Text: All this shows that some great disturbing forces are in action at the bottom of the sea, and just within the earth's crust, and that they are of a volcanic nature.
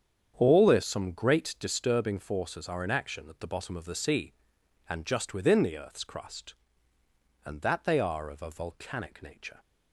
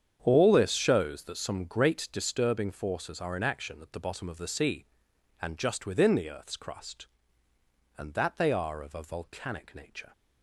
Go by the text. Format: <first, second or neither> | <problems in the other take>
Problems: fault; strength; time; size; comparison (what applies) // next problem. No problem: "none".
second | starts louder than the rest; strong; until 1.3 s; 8 dB; strong in the second // skips "shows that"; at 0.8 s